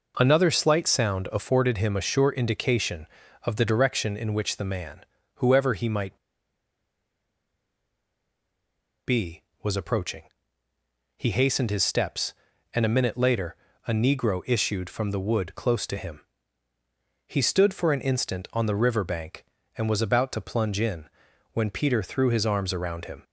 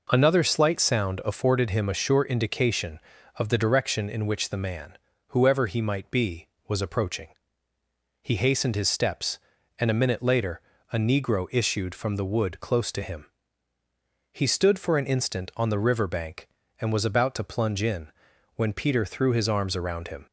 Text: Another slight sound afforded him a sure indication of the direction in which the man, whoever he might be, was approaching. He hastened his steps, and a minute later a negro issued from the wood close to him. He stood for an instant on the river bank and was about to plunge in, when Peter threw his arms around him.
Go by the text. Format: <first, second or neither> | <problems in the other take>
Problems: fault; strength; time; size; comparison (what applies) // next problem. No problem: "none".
second | pauses between "might" and "be"; strong; at 6.1 s; 2.8 s long // pauses between "later" and "a"; slight; at 13.5 s; 0.32 s long; slight in the second